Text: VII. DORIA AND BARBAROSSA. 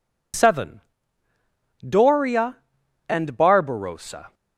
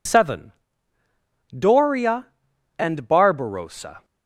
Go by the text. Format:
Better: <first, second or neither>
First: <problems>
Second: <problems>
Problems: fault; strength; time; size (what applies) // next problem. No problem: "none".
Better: neither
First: none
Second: none